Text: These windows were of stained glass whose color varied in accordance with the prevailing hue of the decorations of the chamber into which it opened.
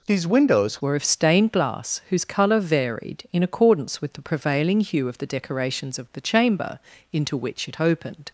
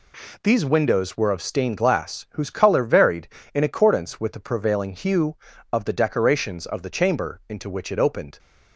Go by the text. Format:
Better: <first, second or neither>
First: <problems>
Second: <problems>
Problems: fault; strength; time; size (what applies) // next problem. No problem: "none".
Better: second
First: changes voice at "were"; from 0.8 s on; 7.4 s long // pauses between "chamber" and "into"; slight; at 6.7 s; 0.34 s long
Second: none